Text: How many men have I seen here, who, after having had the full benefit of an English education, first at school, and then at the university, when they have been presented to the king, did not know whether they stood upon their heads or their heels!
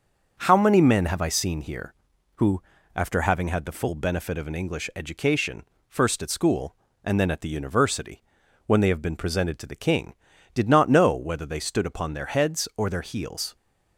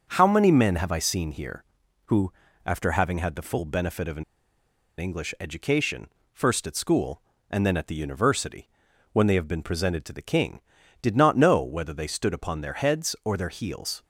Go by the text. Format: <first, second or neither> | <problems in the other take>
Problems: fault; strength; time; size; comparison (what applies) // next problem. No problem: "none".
first | starts louder than the rest; until 1.0 s; 6.5 dB; also in the first // pauses between "an" and "English"; noticeable; at 4.2 s; 0.75 s long